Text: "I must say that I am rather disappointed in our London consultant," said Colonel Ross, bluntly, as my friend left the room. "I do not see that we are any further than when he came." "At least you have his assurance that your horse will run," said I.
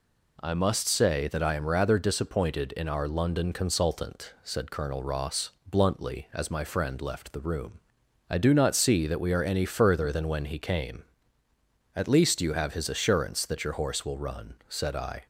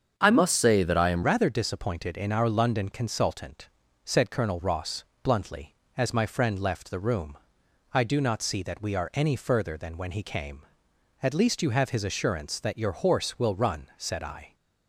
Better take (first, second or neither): first